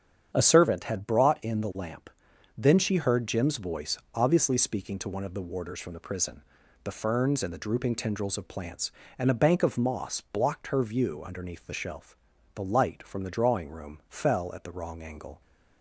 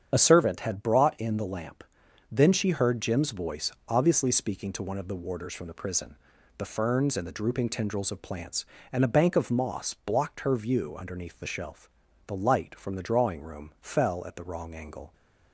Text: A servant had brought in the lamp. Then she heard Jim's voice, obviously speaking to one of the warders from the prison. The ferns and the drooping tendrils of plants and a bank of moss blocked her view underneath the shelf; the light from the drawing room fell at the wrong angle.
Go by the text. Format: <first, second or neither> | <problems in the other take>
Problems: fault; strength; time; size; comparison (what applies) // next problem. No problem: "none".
first | loses the start of "A"; at 0.1 s; 30 ms // starts louder than the rest; strong; until 1.1 s; 8 dB; strong in the first